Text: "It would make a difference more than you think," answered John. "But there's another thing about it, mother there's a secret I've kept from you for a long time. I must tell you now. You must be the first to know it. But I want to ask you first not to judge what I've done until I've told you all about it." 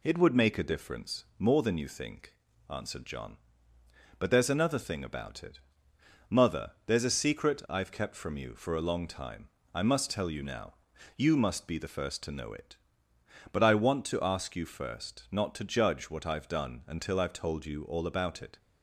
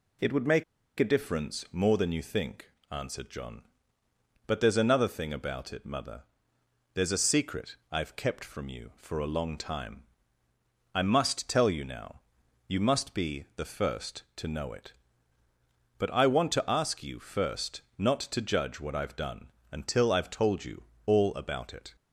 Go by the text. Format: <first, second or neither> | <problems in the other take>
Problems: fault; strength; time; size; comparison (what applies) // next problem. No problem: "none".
first | pauses between "make" and "a"; slight; at 0.6 s; 0.35 s long // pauses between "mother" and "there's"; noticeable; at 6.2 s; 0.70 s long; slight in the first // pauses between "secret" and "I've"; slight; at 7.7 s; 0.16 s long // pauses between "first" and "not"; slight; at 17.8 s; 0.16 s long // pauses between "done" and "until"; slight; at 19.4 s; 0.24 s long // pauses between "you" and "all"; slight; at 20.8 s; 0.24 s long